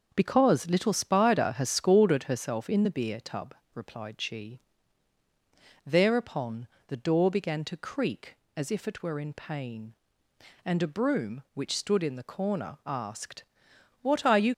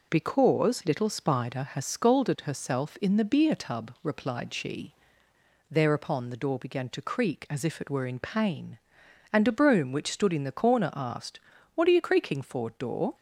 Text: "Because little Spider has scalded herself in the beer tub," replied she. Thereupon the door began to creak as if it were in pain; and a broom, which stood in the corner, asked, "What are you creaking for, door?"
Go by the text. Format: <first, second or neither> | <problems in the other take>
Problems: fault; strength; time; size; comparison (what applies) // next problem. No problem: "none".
second | starts louder than the rest; noticeable; until 1.1 s; 6 dB // pauses between "Thereupon" and "the"; slight; at 6.6 s; 0.22 s long // stops before "creaking for door"; at 14.5 s